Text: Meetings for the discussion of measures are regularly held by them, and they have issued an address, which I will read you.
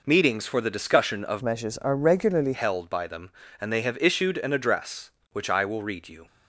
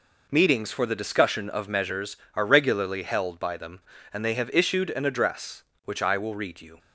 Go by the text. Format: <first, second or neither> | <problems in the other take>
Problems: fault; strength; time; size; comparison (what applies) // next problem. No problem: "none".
second | changes voice from "measures" to "regularly"; from 1.4 to 2.5 s; 1.1 s long